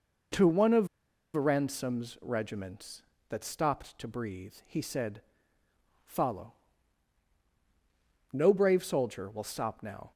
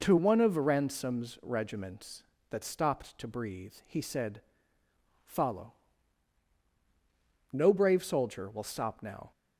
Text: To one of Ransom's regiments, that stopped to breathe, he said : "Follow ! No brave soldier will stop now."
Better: second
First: pauses between "of" and "Ransom's"; noticeable; at 0.8 s; 0.47 s long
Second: none

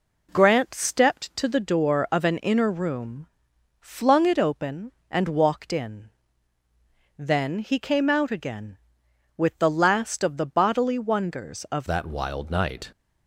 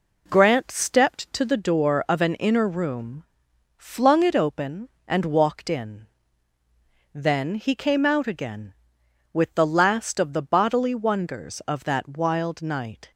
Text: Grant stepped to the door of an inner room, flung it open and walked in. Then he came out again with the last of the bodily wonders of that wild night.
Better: second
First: changes voice at "that"; from 11.8 s on; 1.1 s long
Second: none

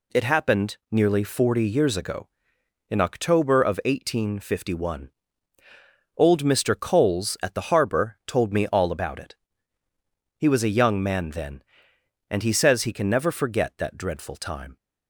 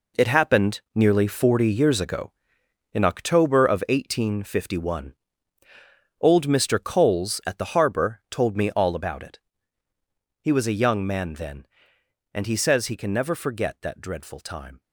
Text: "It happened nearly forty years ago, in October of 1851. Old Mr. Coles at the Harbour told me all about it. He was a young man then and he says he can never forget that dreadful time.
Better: first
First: none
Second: gets quieter; strong; throughout; 10.5 dB

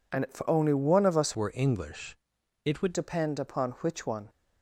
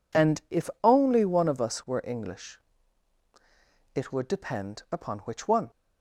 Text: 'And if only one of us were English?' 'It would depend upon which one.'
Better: second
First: changes voice from "were" to "would"; from 1.3 to 2.9 s; 1.6 s long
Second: none

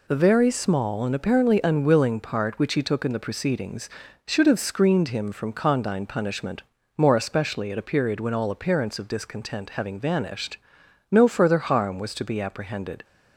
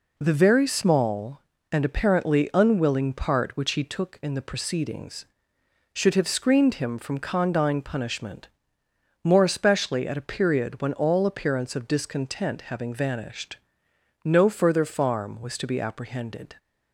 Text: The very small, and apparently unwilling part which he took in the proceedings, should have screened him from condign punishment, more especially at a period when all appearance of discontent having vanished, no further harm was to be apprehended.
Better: first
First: none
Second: says "farm" for "harm"; at 14.8 s

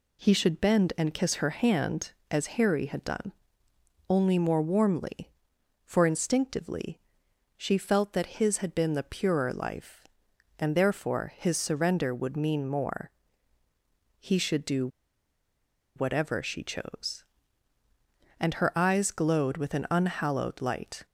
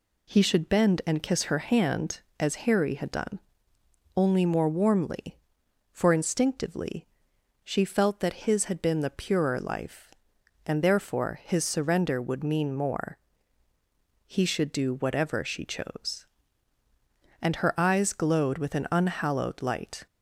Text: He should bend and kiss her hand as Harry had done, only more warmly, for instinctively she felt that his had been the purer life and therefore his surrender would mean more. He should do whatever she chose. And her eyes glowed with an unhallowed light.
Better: second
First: pauses between "instinctively" and "she"; noticeable; at 6.9 s; 0.56 s long // pauses between "do" and "whatever"; at 14.8 s; 1.0 s long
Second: pauses between "instinctively" and "she"; noticeable; at 7.0 s; 0.56 s long

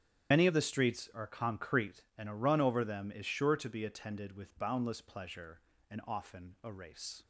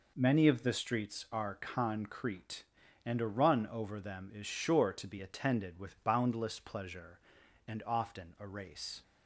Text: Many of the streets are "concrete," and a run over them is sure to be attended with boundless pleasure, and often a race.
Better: second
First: loses the start of "Many"; at 0.3 s; 90 ms // starts louder than the rest; strong; until 1.3 s; 9.5 dB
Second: none

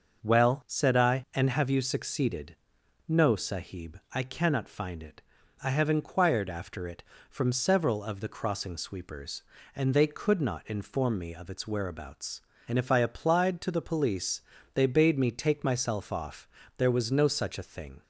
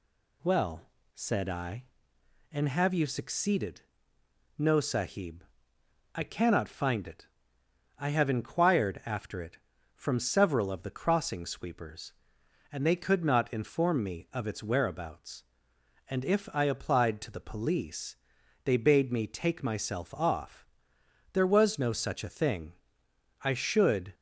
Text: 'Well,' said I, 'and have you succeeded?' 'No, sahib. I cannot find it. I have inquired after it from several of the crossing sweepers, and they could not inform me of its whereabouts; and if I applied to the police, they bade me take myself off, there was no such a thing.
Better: first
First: none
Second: goes on to say "I should"; noticeable; from 23.4 s on; 0.72 s long

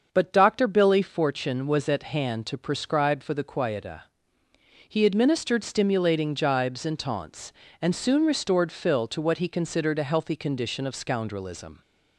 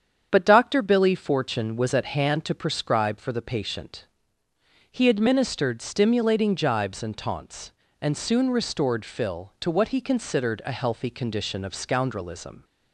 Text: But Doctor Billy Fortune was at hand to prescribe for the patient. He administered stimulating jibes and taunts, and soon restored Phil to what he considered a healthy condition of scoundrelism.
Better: second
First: starts louder than the rest; until 1.1 s; 6.5 dB // says "quieta" for "patient"; at 3.4 s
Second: starts louder than the rest; strong; until 1.3 s; 8 dB

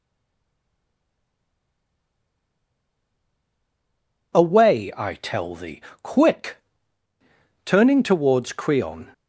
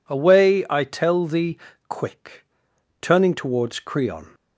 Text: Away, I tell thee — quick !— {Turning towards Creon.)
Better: second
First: stays silent before the first word; strong; until 4.3 s; 4.3 s long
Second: none

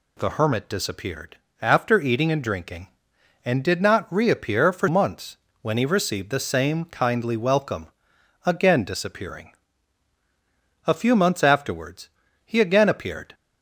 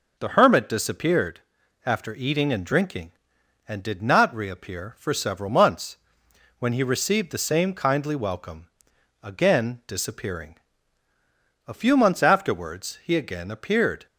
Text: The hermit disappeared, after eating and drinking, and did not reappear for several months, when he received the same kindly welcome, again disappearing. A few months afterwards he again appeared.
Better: second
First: skips "several"; at 4.8 s // pauses between "afterwards" and "he"; slight; at 12.0 s; 0.36 s long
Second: none

